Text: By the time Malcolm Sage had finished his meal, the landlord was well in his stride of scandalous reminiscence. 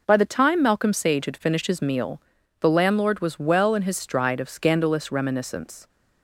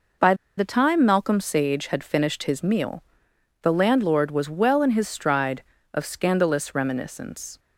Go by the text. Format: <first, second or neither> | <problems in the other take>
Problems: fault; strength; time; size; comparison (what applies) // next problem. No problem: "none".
first | pauses between "By" and "the"; slight; at 0.3 s; 0.23 s long